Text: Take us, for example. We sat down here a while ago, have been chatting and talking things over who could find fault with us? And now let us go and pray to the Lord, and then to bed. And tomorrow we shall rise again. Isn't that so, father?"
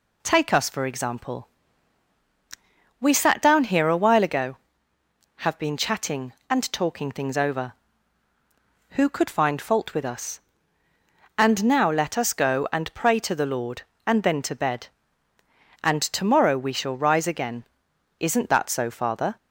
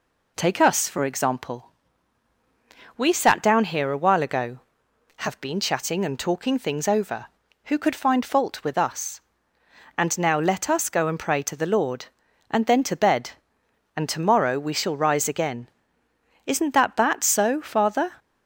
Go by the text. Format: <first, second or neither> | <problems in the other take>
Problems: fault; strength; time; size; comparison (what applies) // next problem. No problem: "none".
first | says "that" twice; at 16.9 s